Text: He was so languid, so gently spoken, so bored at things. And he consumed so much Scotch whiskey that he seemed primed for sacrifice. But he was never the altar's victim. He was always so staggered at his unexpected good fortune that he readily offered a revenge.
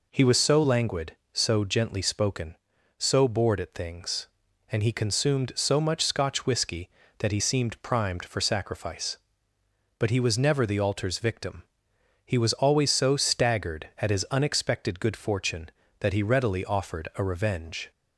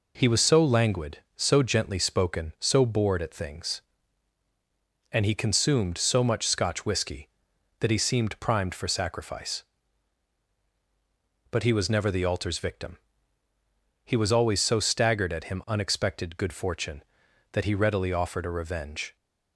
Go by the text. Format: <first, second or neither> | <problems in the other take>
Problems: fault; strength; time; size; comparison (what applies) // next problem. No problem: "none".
first | says "him" for "his"; at 15.5 s